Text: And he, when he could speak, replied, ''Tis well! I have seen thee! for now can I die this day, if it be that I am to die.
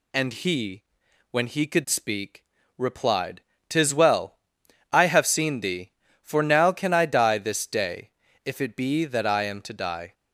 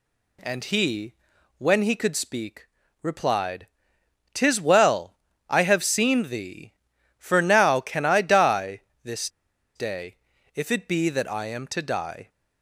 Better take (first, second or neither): first